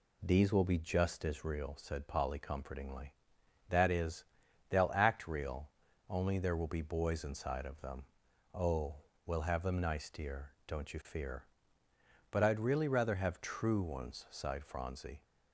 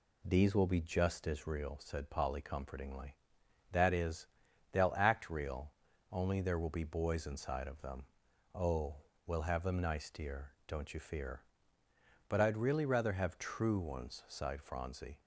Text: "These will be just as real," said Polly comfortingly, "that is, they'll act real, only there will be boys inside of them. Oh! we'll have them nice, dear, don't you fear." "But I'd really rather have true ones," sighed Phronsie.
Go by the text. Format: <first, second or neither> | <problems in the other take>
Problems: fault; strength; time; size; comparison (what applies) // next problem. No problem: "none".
neither | none